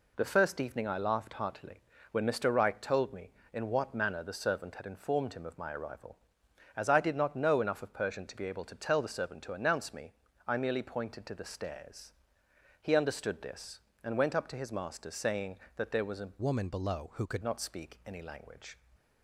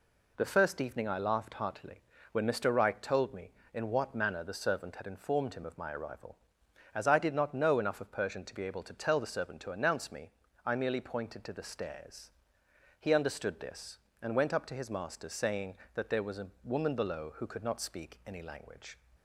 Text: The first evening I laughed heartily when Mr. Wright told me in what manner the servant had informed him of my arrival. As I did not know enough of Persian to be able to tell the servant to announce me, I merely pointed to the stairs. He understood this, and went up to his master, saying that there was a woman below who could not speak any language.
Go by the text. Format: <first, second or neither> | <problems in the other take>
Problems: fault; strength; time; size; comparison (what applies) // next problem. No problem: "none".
second | pauses between "heartily" and "when"; slight; at 1.8 s; 0.32 s long; slight in the second // changes voice from "woman" to "could"; from 16.4 to 17.4 s; 1.0 s long